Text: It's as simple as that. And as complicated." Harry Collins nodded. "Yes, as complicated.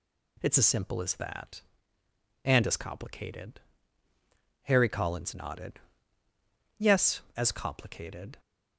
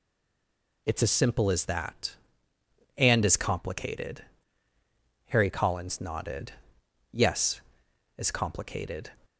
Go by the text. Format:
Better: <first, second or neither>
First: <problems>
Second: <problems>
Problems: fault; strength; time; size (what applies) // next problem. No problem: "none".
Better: first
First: none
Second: stays silent before the first word; slight; until 0.8 s; 0.8 s long